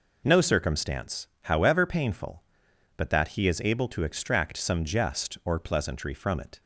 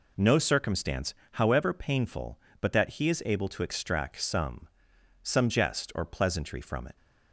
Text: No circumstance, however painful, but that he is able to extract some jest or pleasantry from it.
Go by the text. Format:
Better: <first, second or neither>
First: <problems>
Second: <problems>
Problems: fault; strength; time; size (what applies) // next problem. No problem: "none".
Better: first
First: none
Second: says "some" twice; at 5.2 s